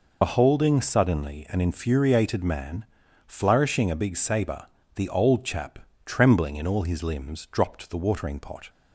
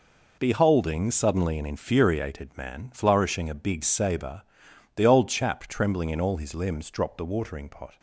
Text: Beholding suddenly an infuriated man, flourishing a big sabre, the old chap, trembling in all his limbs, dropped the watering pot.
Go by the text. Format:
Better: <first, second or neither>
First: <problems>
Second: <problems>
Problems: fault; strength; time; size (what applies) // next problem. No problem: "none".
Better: second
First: loses the start of "Beholding"; at 0.2 s; 60 ms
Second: none